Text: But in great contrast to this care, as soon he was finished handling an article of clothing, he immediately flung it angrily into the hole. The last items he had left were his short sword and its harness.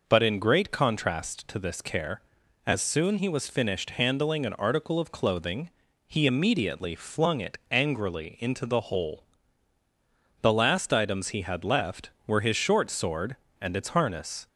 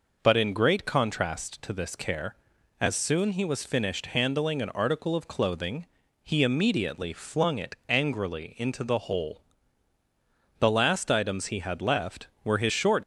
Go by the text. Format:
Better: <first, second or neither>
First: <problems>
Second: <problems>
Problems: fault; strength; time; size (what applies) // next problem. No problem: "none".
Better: first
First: none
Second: stops before "sword and its harness"; at 13.0 s